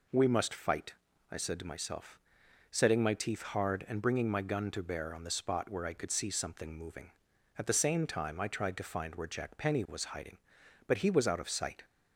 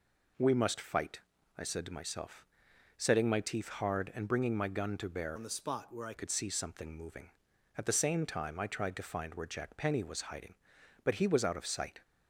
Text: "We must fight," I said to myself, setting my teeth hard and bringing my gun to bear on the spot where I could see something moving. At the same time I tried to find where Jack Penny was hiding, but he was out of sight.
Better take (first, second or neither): first